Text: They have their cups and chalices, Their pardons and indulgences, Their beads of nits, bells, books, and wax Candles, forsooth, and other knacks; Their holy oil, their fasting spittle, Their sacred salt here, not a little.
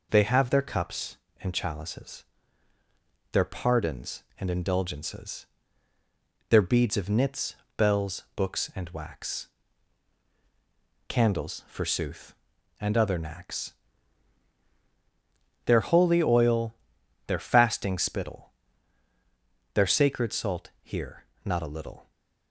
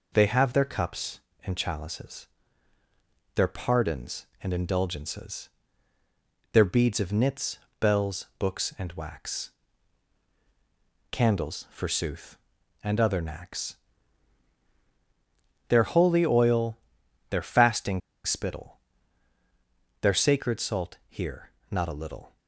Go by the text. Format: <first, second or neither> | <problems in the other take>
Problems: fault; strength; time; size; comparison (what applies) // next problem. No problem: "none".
first | pauses between "wax" and "Candles"; strong; at 9.5 s; 1.6 s long; strong in the first // pauses between "fasting" and "spittle"; slight; at 18.0 s; 0.26 s long